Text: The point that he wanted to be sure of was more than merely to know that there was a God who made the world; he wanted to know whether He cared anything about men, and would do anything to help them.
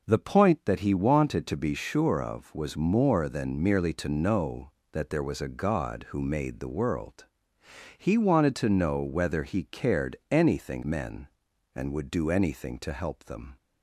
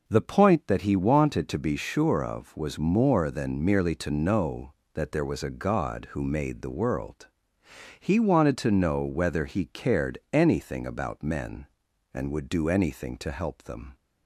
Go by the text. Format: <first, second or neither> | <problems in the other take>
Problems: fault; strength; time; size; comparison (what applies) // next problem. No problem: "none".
second | skips "about"; at 10.8 s